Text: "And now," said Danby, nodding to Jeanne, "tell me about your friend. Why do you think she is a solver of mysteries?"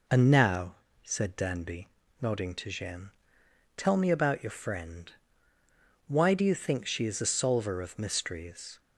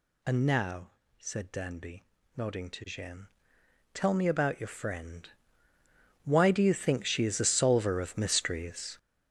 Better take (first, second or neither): first